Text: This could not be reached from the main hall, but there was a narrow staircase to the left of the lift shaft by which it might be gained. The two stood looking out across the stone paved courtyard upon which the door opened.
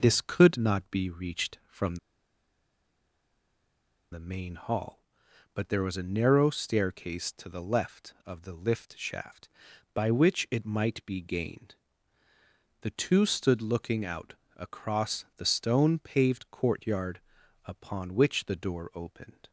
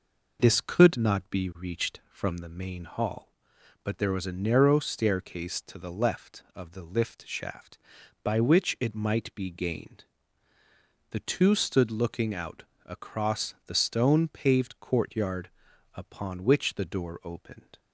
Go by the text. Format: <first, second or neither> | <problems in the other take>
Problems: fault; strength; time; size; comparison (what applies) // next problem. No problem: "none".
second | pauses between "from" and "the"; strong; at 1.9 s; 2.1 s long // pauses between "out" and "across"; slight; at 14.3 s; 0.20 s long; slight in the second // pauses between "courtyard" and "upon"; noticeable; at 17.1 s; 0.46 s long; noticeable in the second